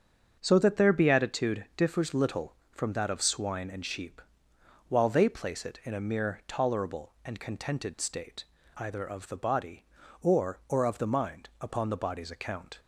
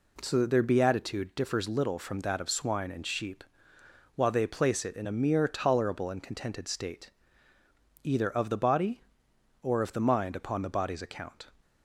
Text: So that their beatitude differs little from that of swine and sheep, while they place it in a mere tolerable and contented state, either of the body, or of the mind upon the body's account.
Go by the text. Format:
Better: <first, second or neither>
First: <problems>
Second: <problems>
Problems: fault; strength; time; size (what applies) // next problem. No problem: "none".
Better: second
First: starts louder than the rest; until 1.4 s; 7 dB // says "or" twice; at 10.6 s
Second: none